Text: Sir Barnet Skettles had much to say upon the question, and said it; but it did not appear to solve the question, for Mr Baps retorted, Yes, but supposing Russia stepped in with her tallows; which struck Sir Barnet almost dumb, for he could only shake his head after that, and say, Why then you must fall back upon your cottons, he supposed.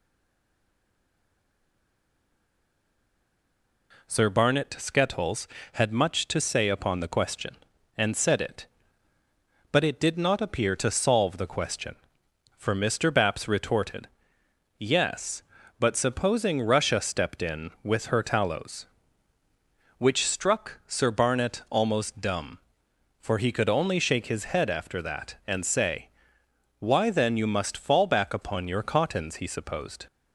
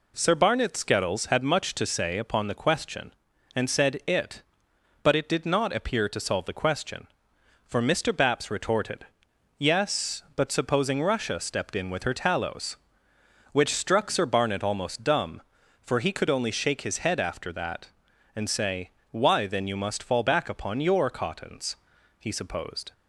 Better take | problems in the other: second | stays silent before the first word; strong; until 3.9 s; 3.9 s long

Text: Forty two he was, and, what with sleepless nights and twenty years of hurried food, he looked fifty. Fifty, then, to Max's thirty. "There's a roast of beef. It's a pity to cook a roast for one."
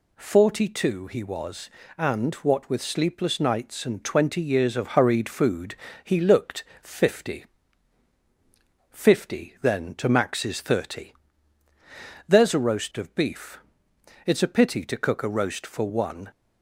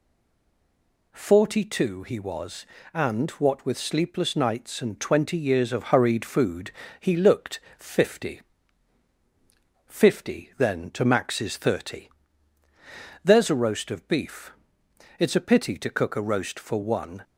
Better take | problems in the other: first | stays silent before the first word; until 1.1 s; 1.1 s long // pauses between "looked" and "fifty"; slight; at 7.5 s; 0.18 s long; slight in the first

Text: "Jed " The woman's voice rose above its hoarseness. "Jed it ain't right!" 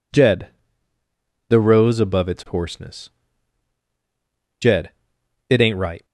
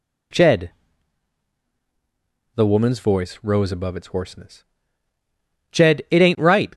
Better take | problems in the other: second | skips "woman's voice"; at 1.6 s // pauses between "Jed" and "it"; noticeable; at 4.9 s; 0.58 s long

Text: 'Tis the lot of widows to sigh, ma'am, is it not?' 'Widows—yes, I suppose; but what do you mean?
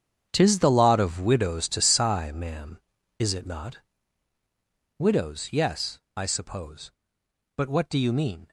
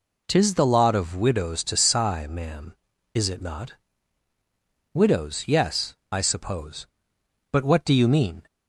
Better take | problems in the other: second | gets quieter; strong; throughout; 13 dB

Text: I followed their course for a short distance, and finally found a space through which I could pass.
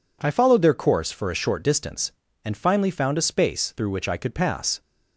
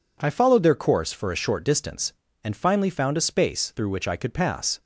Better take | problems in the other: neither | none

